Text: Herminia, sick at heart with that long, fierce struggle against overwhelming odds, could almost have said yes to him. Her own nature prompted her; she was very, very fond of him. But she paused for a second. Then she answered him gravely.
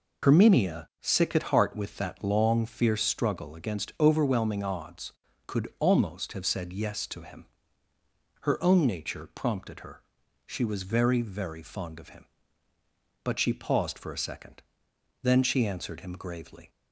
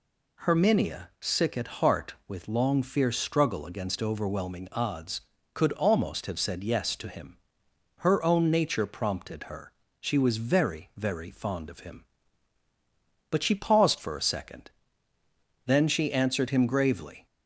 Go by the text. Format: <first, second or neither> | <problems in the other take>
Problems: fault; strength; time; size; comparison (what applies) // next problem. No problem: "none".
first | skips "that"; at 2.4 s